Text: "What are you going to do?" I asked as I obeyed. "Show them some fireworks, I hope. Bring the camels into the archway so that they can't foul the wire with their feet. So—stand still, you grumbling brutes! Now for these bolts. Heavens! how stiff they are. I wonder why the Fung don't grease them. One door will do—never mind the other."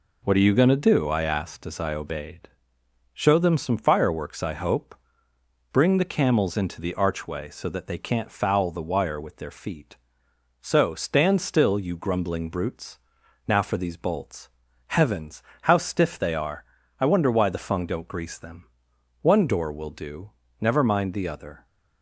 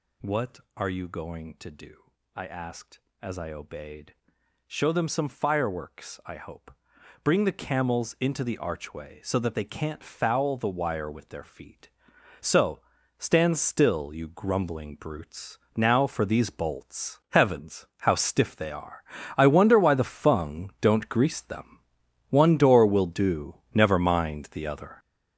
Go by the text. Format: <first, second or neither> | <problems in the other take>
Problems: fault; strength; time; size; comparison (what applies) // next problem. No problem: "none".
first | gets louder; strong; throughout; 9.5 dB